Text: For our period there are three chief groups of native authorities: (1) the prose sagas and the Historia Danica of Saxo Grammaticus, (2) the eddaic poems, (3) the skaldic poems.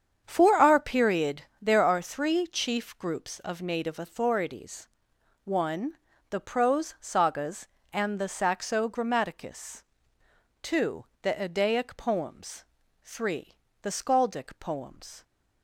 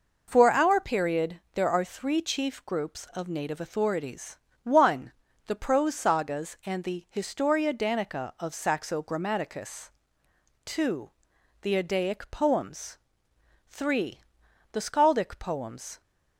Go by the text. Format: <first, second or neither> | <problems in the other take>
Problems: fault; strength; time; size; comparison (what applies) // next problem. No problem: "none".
second | starts louder than the rest; strong; until 1.2 s; 8 dB // pauses between "period" and "there"; slight; at 1.4 s; 0.18 s long; slight in the second // skips "Historia Danica of"; at 8.2 s